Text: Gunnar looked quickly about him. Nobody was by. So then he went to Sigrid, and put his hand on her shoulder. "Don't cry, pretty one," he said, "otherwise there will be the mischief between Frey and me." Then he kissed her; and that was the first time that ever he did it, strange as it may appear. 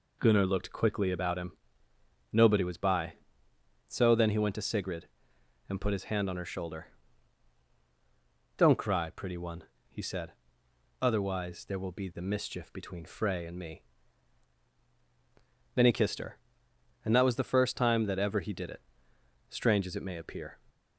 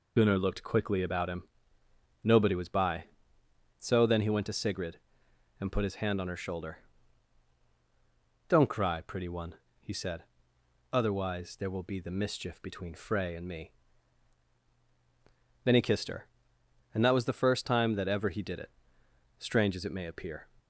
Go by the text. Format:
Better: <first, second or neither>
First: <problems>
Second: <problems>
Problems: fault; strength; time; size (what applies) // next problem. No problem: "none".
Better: first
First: none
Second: loses the start of "Gunnar"; at 0.1 s; 45 ms